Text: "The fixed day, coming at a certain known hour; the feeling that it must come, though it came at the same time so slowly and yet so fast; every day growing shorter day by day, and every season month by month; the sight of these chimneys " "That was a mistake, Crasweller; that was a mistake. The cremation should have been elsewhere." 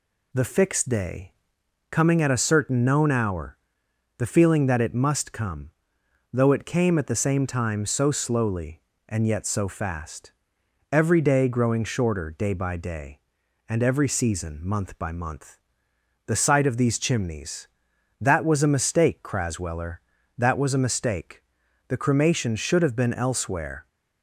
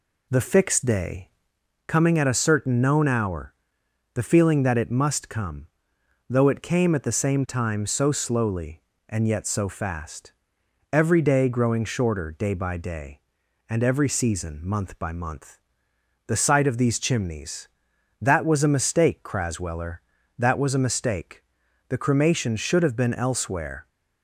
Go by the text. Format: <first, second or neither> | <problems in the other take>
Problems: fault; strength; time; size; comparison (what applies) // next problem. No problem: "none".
first | starts louder than the rest; slight; until 1.5 s; 2 dB